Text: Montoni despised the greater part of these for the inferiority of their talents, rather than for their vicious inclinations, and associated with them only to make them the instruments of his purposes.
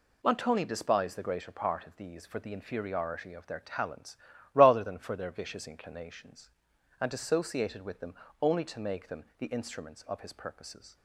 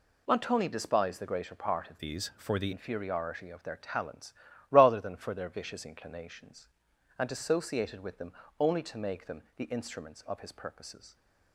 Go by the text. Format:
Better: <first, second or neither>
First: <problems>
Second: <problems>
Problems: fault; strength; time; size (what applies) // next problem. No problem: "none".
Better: first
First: pauses between "them" and "only"; slight; at 8.1 s; 0.28 s long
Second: changes voice from "these" to "the"; from 1.9 to 2.7 s; 0.8 s long // pauses between "them" and "only"; slight; at 8.3 s; 0.28 s long